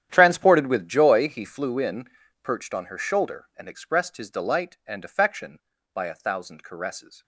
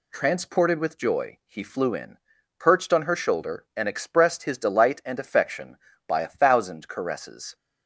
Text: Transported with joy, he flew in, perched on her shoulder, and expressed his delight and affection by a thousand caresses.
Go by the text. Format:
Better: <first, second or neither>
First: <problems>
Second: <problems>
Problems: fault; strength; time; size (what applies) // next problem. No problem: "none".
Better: second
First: gets quieter; strong; throughout; 17 dB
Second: none